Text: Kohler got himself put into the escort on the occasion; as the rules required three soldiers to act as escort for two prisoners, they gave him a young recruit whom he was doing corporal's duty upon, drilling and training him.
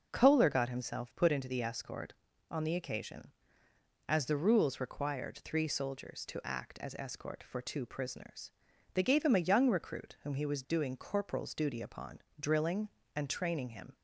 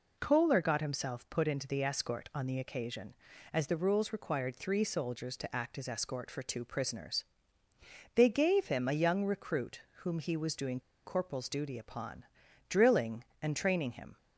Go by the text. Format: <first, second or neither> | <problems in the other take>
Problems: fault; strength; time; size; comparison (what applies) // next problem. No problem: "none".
first | pauses between "recruit" and "whom"; slight; at 9.8 s; 0.20 s long // pauses between "doing" and "corporal's"; slight; at 10.7 s; 0.25 s long